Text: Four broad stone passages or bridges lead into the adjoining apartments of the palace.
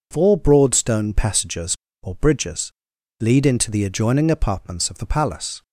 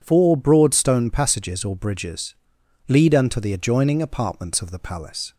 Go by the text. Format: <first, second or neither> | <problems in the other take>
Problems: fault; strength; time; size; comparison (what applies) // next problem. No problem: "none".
first | pauses between "bridges" and "lead"; noticeable; at 2.3 s; 0.56 s long; noticeable in the first // says "unto" for "into"; at 3.1 s